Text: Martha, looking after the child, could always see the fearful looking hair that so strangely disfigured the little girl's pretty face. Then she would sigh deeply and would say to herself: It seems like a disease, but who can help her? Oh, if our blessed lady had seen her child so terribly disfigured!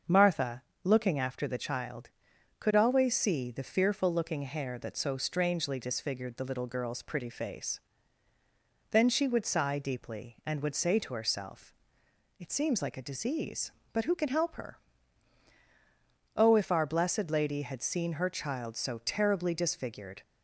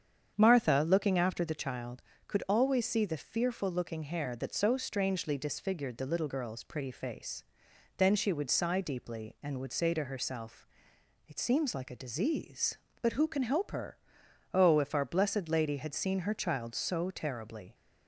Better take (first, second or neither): first